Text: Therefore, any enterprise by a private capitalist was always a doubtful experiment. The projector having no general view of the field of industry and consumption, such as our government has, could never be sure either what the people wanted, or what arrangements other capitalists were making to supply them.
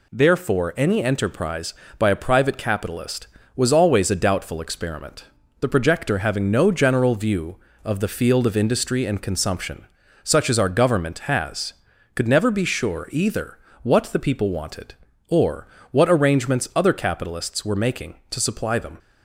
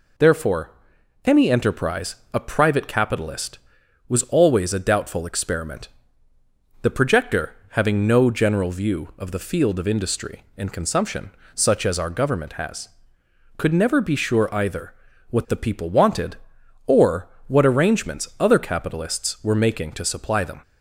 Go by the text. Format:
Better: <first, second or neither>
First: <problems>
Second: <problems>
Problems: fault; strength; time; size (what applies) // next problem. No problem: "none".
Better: first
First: pauses between "either" and "what"; slight; at 13.5 s; 0.24 s long // pauses between "or" and "what"; slight; at 15.6 s; 0.24 s long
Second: skips "by"; at 2.2 s // pauses between "projector" and "having"; slight; at 7.5 s; 0.16 s long // pauses between "either" and "what"; at 14.9 s; 0.38 s long // pauses between "or" and "what"; slight; at 17.2 s; 0.20 s long